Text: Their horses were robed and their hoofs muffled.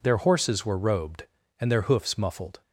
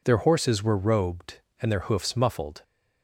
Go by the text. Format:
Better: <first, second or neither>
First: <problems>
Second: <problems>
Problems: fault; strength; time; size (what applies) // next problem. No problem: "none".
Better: neither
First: none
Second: none